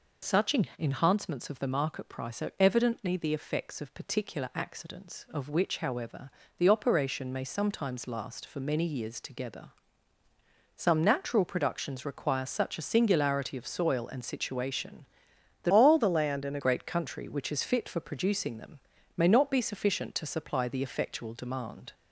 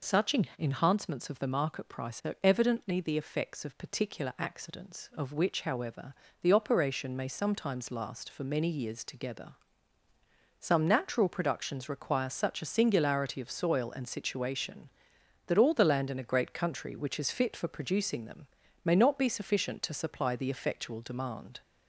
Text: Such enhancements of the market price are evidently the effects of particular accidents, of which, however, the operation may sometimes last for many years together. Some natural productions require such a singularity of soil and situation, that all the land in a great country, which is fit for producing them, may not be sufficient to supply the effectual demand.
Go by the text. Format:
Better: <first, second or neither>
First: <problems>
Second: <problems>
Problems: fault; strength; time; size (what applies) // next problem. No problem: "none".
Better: second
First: pauses between "Such" and "enhancements"; slight; at 0.5 s; 0.24 s long // changes voice from "all" to "a"; from 15.7 to 16.5 s; 0.8 s long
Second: pauses between "Such" and "enhancements"; slight; at 0.3 s; 0.24 s long